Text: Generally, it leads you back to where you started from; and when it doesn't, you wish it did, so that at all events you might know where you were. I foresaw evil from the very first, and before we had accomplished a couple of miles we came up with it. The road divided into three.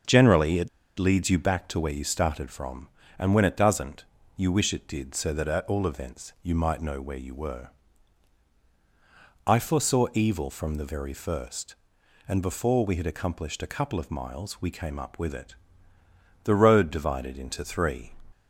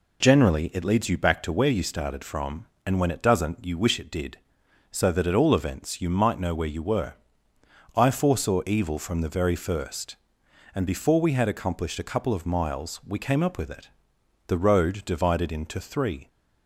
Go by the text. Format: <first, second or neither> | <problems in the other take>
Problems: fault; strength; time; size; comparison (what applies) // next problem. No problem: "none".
second | starts louder than the rest; until 1.3 s; 7 dB // pauses between "it" and "leads"; slight; at 0.6 s; 0.30 s long